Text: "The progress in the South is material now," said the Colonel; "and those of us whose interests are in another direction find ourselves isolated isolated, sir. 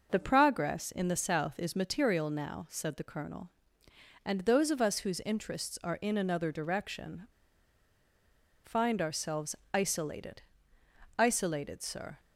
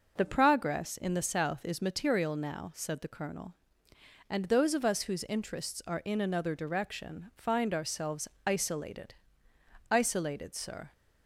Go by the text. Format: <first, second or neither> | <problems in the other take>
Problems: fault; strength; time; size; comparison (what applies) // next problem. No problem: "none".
second | pauses between "direction" and "find"; strong; at 7.2 s; 1.3 s long // pauses between "ourselves" and "isolated"; slight; at 9.5 s; 0.18 s long; slight in the second // pauses between "isolated" and "isolated"; noticeable; at 10.4 s; 0.74 s long; noticeable in the second